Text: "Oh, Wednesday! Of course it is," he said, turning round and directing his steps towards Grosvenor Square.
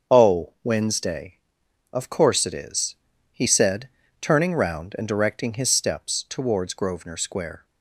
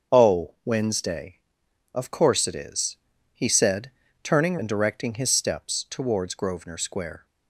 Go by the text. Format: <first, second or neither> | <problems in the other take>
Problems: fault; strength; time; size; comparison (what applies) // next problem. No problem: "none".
first | starts louder than the rest; until 1.2 s; 7 dB; also in the first // skips "round"; at 4.5 s